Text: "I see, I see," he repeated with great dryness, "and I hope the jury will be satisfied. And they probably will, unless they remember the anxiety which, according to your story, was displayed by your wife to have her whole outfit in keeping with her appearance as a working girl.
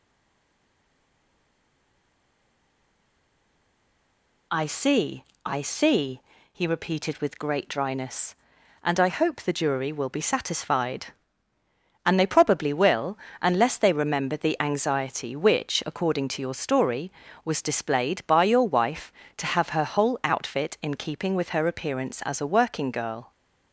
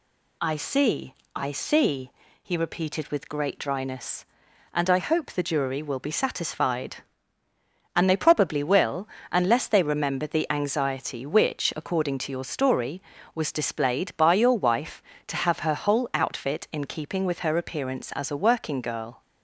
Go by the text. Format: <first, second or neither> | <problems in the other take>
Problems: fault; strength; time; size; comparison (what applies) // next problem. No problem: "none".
second | stays silent before the first word; strong; until 4.5 s; 4.5 s long